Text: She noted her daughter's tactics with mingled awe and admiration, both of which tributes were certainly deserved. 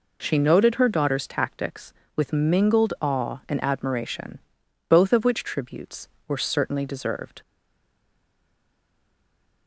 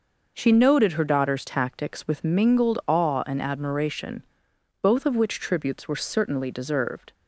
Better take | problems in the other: second | stays silent after the last word; from 7.4 s on; 2.2 s long

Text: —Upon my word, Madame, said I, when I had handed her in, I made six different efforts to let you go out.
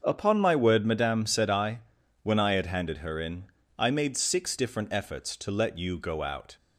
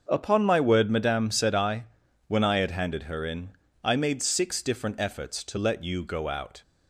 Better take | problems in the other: neither | starts louder than the rest; the same in both

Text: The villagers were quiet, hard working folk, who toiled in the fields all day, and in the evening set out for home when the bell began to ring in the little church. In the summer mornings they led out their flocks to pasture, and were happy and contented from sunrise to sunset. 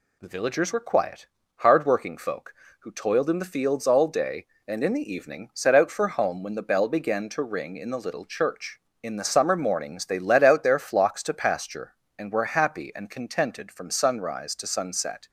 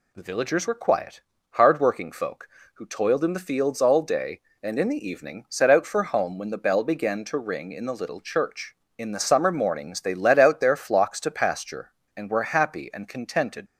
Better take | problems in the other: first | stops before "from sunrise to sunset"; at 13.6 s

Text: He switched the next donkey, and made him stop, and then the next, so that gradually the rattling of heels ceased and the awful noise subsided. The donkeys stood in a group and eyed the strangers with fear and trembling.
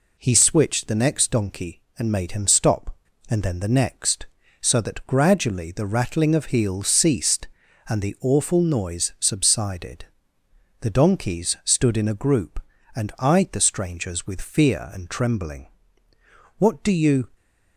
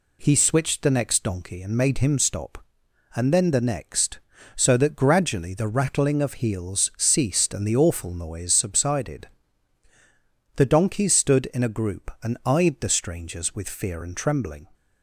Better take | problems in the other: second | goes on to say "What do you"; noticeable; from 16.5 s on; 0.72 s long

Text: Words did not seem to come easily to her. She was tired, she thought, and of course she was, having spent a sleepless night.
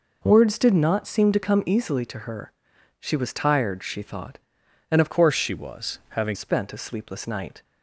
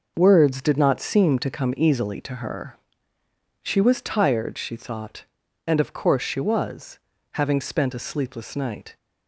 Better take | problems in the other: second | changes voice from "course" to "having"; from 5.1 to 6.3 s; 1.2 s long

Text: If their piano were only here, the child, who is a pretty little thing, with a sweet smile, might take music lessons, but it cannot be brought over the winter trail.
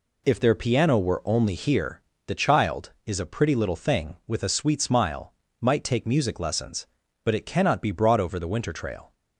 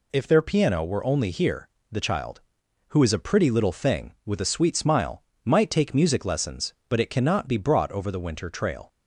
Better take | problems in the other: second | skips "who"; at 2.9 s

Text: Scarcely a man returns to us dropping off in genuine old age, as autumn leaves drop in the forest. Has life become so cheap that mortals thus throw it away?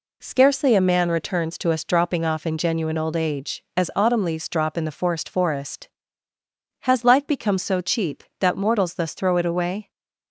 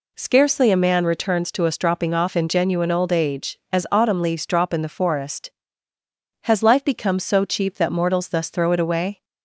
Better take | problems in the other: second | says "forest" twice; at 5.3 s

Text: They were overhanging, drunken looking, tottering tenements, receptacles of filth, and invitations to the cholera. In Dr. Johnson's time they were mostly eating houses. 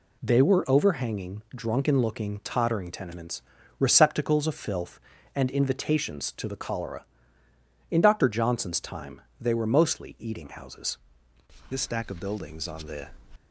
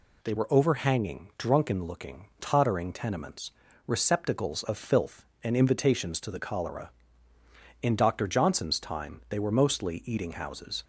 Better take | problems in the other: second | pauses between "time" and "they"; slight; at 9.2 s; 0.20 s long // goes on to say "This stack of buildings on the"; from 11.6 s on; 1.4 s long

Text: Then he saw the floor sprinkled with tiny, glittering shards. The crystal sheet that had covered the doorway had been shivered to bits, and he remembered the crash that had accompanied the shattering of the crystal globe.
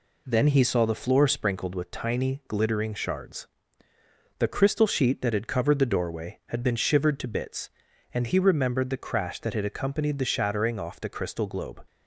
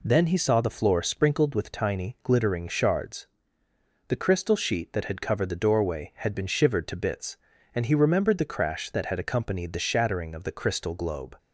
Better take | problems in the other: second | says "off" for "of"; at 10.7 s

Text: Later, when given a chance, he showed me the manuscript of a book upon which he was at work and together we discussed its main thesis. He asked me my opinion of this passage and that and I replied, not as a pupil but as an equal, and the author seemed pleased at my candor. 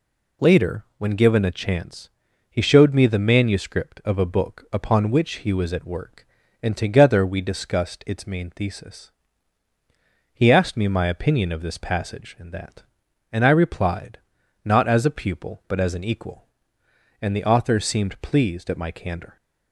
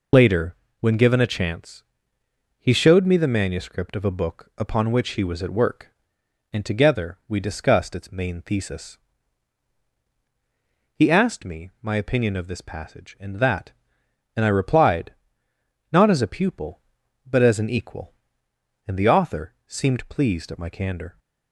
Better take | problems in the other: first | loses the start of "Later"; at 0.1 s; 30 ms

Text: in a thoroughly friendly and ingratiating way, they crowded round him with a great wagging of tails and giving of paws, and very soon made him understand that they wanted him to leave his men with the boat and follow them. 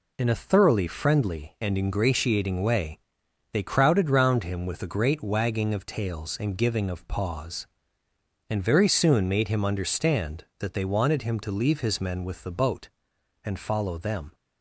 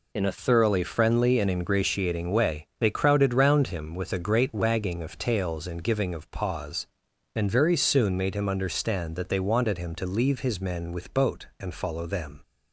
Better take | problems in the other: first | skips "the"; at 11.1 s

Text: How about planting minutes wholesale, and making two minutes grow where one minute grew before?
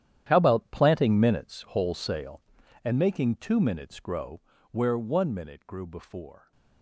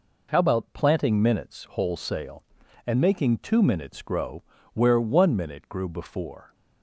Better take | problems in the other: second | gets quieter; strong; throughout; 15.5 dB // pauses between "grow" and "where"; slight; at 4.4 s; 0.30 s long; slight in the second

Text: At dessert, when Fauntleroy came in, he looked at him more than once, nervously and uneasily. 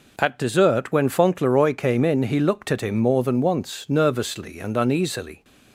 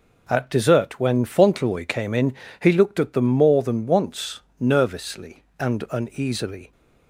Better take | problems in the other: first | says "them" for "him"; at 3.1 s

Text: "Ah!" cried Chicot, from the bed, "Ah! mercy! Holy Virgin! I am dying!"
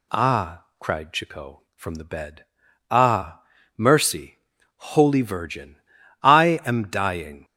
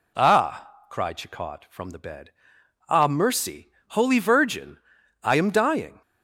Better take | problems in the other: neither | none

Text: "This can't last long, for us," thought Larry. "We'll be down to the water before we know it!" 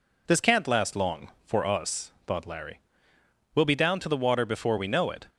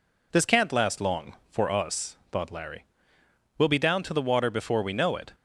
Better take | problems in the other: neither | none

